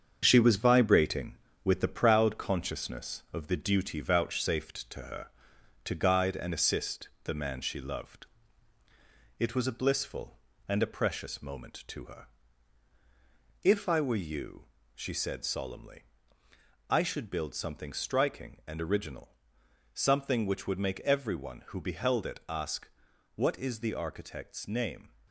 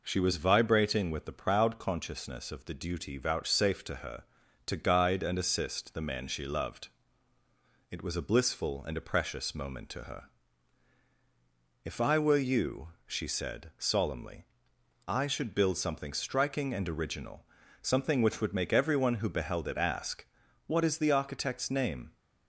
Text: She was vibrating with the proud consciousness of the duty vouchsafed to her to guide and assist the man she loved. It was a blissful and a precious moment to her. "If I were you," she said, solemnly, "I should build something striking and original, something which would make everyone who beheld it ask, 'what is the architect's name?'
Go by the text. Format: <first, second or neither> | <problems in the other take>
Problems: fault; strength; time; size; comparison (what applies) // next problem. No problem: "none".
second | gets quieter; throughout; 6 dB